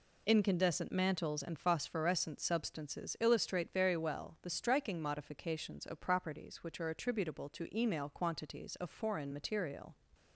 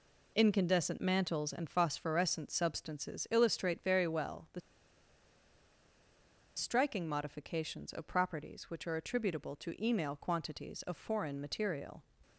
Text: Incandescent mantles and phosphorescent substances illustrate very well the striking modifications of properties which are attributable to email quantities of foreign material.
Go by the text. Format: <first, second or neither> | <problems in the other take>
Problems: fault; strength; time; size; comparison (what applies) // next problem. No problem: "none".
first | pauses between "the" and "striking"; strong; at 4.5 s; 1.9 s long